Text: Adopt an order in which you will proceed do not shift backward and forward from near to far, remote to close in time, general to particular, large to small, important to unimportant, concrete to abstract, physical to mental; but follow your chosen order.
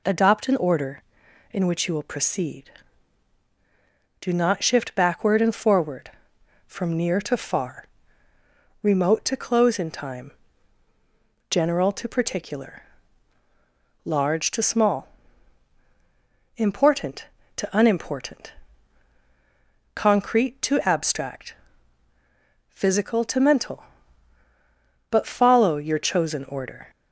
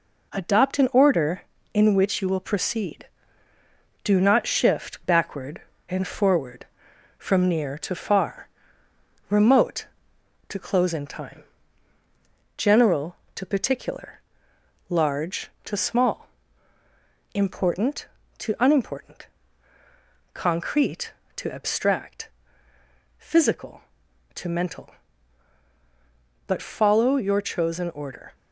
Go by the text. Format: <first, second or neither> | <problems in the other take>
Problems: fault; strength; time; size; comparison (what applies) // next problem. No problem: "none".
first | gets quieter; noticeable; throughout; 4.5 dB